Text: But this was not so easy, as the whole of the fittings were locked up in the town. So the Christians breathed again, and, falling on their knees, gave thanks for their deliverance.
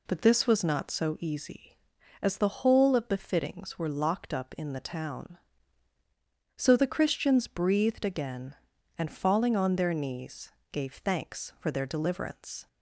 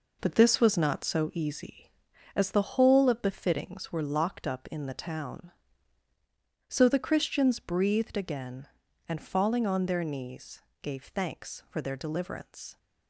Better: first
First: none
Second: gets quieter; strong; throughout; 7.5 dB

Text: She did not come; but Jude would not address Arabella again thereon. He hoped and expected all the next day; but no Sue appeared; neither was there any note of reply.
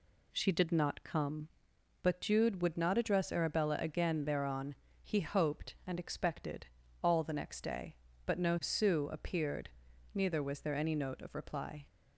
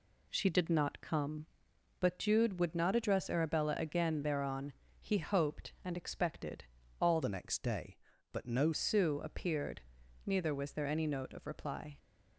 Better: first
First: pauses between "expected" and "all"; slight; at 6.6 s; 0.36 s long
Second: pauses between "expected" and "all"; slight; at 6.6 s; 0.36 s long // changes voice from "the" to "no"; from 7.2 to 8.7 s; 1.5 s long

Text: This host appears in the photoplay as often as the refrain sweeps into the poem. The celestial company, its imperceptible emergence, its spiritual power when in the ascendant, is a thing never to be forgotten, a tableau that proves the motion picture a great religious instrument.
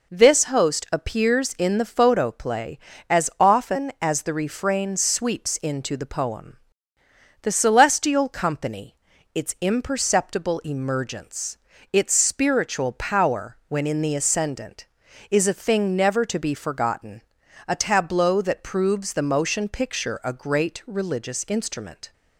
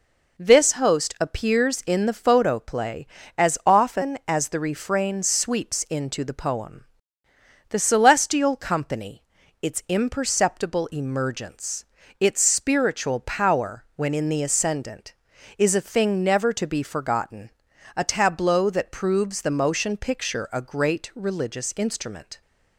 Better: neither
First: none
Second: none

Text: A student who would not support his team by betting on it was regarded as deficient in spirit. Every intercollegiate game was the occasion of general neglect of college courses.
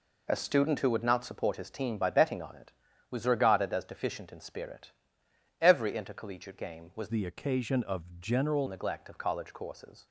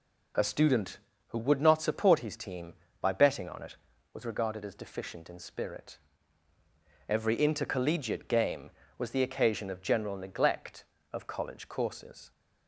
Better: second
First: changes voice from "the" to "general"; from 7.1 to 8.6 s; 1.5 s long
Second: none

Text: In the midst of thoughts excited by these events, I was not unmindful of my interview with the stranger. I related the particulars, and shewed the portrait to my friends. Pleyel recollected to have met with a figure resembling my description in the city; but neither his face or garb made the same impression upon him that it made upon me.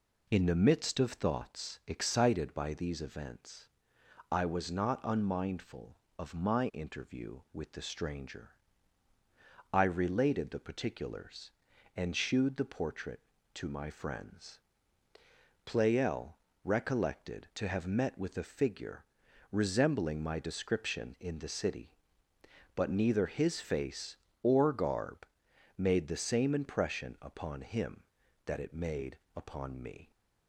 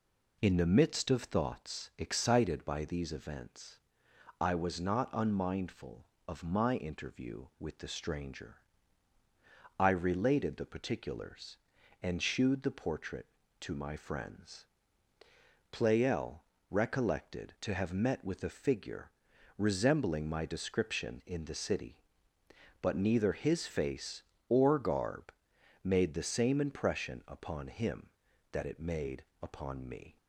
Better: neither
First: pauses between "Pleyel" and "recollected"; slight; at 16.3 s; 0.28 s long // pauses between "figure" and "resembling"; noticeable; at 19.0 s; 0.48 s long // pauses between "garb" and "made"; noticeable; at 25.2 s; 0.50 s long // pauses between "made" and "upon"; slight; at 29.1 s; 0.18 s long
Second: pauses between "Pleyel" and "recollected"; slight; at 16.4 s; 0.28 s long // pauses between "figure" and "resembling"; noticeable; at 19.0 s; 0.48 s long // pauses between "garb" and "made"; noticeable; at 25.3 s; 0.50 s long // pauses between "made" and "upon"; slight; at 29.2 s; 0.18 s long

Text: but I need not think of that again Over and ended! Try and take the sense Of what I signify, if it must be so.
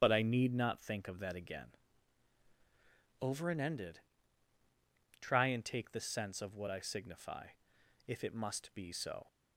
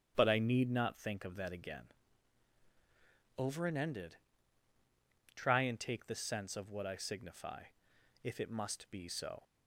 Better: second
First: loses the start of "but"; at 0.0 s; 35 ms // starts louder than the rest; strong; until 1.0 s; 9 dB // pauses between "again" and "Over"; strong; at 1.6 s; 1.5 s long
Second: starts louder than the rest; strong; until 1.1 s; 9 dB // pauses between "again" and "Over"; strong; at 1.8 s; 1.5 s long

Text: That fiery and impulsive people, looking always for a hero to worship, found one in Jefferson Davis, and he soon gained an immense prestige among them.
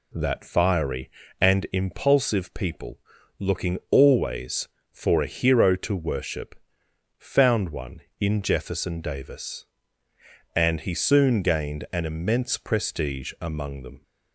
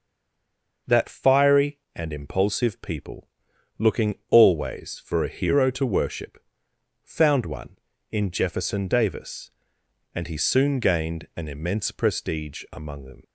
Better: first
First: none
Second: stays silent before the first word; slight; until 0.8 s; 0.8 s long // pauses between "looking" and "always"; slight; at 4.1 s; 0.16 s long

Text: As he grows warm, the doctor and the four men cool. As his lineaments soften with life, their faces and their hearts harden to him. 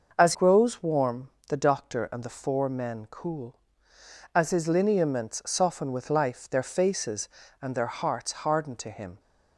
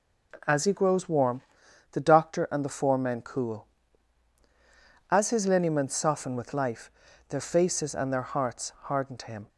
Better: second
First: starts louder than the rest; noticeable; until 1.1 s; 6 dB // skips "he"; at 0.3 s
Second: none

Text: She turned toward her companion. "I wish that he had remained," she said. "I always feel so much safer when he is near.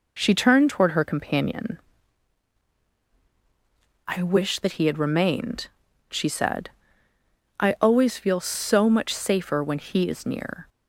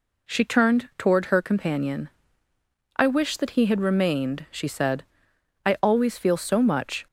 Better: first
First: none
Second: stops before "safer when he is near"; at 7.0 s

